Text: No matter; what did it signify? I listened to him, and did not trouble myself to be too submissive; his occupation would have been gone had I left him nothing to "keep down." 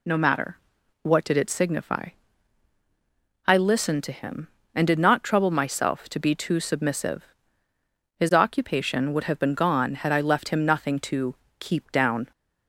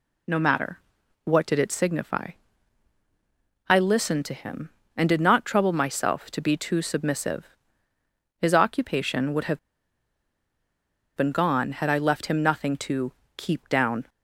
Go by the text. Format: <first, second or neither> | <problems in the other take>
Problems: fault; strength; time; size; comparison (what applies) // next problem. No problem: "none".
first | pauses between "have" and "been"; strong; at 9.5 s; 1.5 s long // pauses between "to" and "keep"; slight; at 13.1 s; 0.24 s long; slight in the first